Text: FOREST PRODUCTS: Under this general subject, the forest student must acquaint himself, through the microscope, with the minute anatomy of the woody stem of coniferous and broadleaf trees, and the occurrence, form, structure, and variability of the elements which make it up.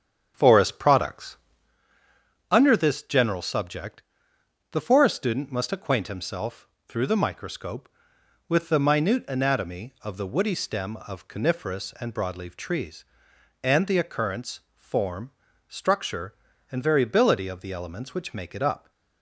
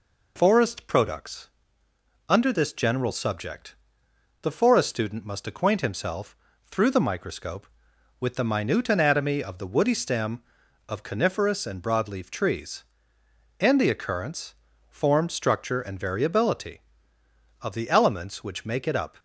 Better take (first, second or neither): second